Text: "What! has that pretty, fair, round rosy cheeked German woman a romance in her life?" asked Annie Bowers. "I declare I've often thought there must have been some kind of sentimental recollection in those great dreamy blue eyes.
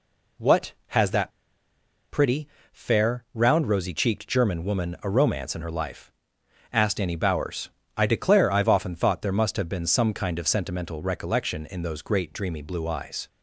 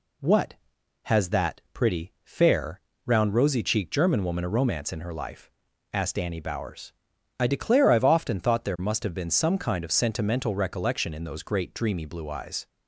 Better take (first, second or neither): second